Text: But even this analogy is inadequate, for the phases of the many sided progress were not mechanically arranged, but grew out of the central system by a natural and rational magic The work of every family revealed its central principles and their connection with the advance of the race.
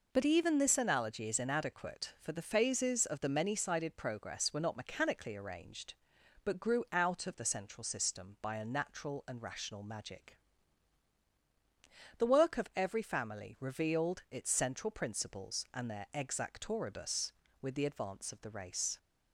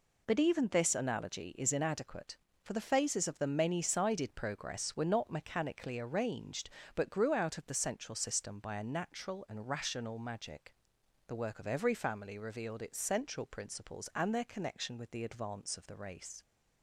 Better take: second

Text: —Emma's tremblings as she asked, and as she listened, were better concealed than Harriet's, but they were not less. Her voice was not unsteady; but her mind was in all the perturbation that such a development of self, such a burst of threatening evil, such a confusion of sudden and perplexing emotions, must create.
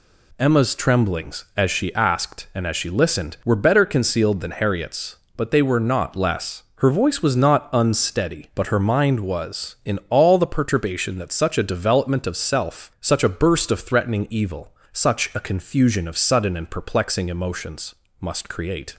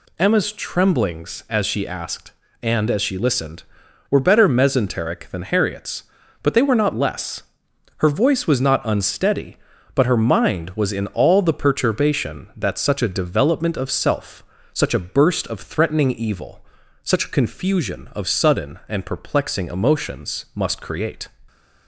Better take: first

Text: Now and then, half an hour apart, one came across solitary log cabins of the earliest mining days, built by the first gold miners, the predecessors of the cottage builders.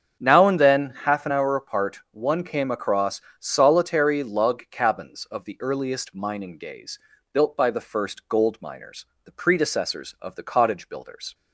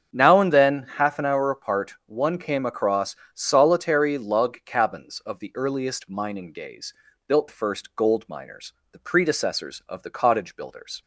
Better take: first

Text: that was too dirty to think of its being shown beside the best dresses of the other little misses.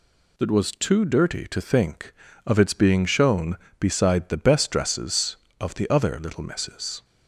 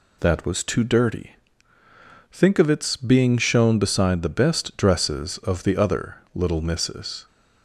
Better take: first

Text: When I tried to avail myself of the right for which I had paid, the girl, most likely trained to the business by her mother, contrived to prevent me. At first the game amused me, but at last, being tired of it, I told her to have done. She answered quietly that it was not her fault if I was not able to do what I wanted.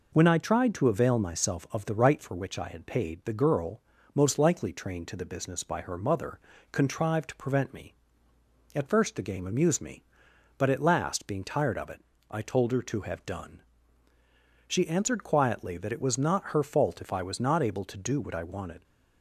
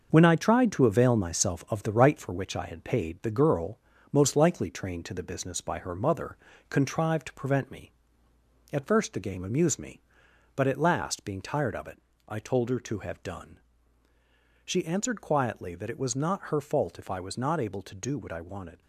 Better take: first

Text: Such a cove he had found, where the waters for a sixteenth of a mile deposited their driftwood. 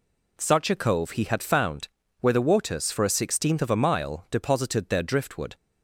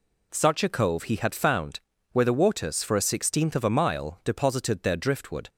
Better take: neither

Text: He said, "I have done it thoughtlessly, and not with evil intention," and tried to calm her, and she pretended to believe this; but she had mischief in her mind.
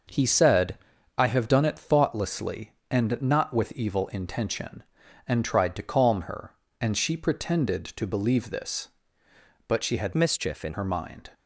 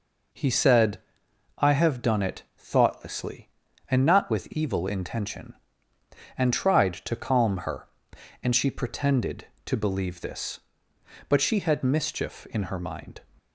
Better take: second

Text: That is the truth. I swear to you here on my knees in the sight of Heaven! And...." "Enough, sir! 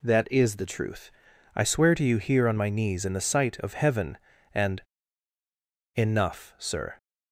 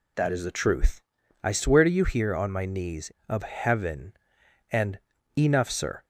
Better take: first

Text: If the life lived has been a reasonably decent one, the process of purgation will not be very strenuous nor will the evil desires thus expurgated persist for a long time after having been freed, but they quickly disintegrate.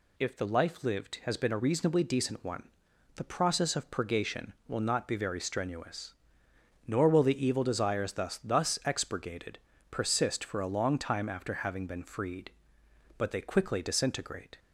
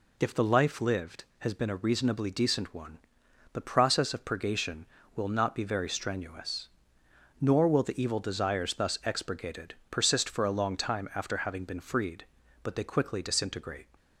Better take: second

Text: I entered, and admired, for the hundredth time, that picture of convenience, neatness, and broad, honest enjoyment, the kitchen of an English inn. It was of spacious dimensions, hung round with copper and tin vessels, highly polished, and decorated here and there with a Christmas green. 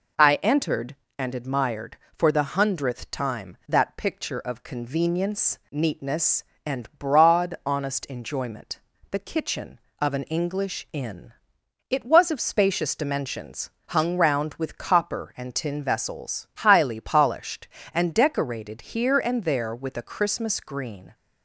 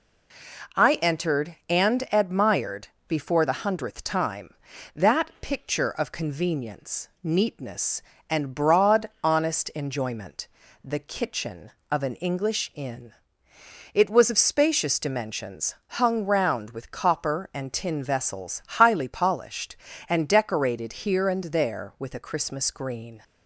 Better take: first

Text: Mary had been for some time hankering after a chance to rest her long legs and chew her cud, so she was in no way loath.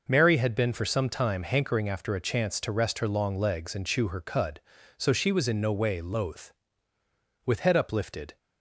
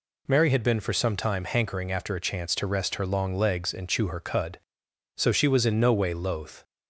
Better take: second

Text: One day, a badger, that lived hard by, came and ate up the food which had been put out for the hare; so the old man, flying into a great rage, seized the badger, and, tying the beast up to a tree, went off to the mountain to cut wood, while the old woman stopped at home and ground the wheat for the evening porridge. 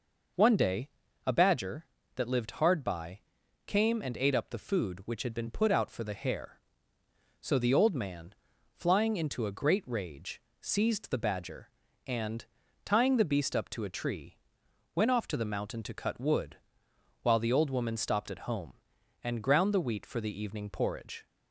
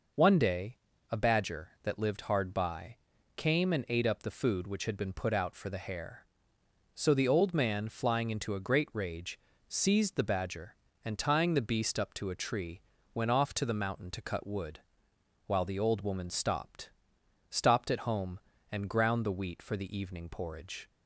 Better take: first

